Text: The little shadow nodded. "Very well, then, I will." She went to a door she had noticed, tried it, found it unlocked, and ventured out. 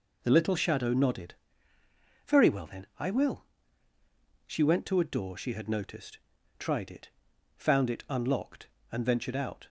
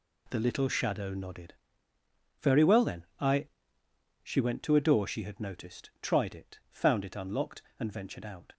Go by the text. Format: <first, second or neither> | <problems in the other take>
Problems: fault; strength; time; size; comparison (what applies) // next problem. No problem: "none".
first | skips "will"; at 3.8 s